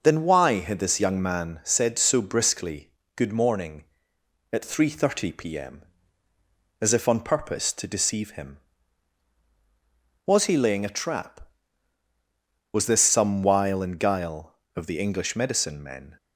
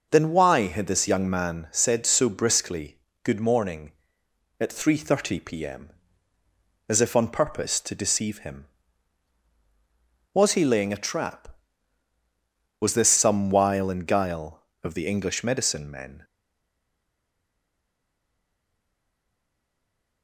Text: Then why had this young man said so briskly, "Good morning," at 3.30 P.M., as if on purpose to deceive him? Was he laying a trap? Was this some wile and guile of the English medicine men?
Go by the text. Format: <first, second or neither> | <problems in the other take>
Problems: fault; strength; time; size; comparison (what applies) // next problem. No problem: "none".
first | stays silent after the last word; strong; from 16.2 s on; 4.0 s long